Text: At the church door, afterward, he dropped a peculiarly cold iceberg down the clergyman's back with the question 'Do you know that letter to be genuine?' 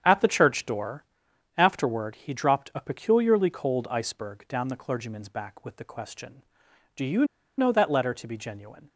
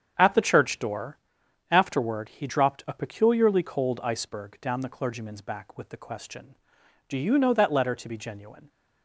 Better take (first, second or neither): second